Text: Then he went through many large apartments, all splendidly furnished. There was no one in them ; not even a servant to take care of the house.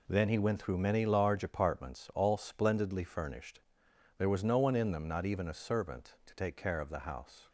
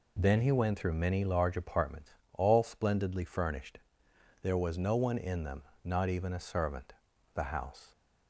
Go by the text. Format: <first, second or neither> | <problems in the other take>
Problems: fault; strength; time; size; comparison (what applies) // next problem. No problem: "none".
first | skips "to take care of"; at 7.1 s